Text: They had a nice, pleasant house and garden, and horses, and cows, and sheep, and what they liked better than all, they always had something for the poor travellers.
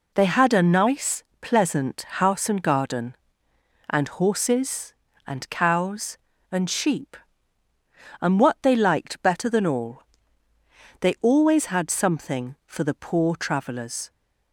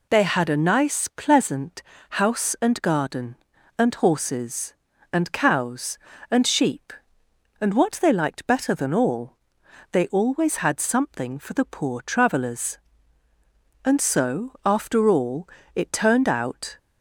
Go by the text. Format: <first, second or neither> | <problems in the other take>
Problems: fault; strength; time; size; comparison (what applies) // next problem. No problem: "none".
first | pauses between "pleasant" and "house"; slight; at 1.8 s; 0.28 s long // goes on to say "And so after all it turned out"; strong; from 13.8 s on; 2.9 s long